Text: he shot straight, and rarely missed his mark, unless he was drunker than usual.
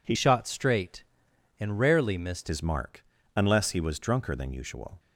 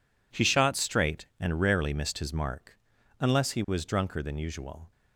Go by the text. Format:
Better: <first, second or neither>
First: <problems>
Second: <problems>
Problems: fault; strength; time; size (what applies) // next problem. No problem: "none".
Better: second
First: changes voice from "shot" to "missed"; from 0.1 to 2.5 s; 2.4 s long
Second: none